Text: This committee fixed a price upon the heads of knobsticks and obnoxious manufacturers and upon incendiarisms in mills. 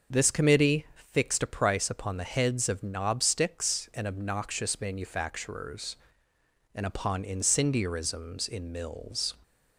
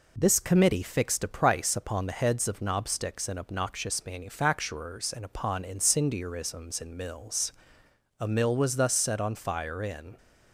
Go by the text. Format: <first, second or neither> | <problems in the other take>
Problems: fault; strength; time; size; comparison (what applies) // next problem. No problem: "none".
first | goes on to say "A mill was thus set on fire in"; strong; from 8.1 s on; 1.9 s long